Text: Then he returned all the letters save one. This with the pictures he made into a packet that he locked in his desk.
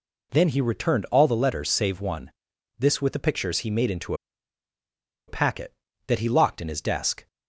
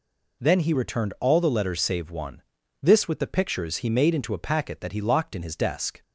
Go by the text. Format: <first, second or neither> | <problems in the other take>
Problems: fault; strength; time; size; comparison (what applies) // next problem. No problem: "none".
second | pauses between "into" and "a"; at 4.1 s; 1.1 s long